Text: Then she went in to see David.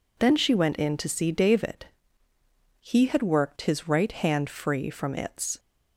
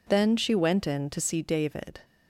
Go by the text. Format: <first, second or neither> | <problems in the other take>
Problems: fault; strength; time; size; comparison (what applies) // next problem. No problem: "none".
second | goes on to say "He had worked his right hand free from its"; strong; from 2.7 s on; 2.7 s long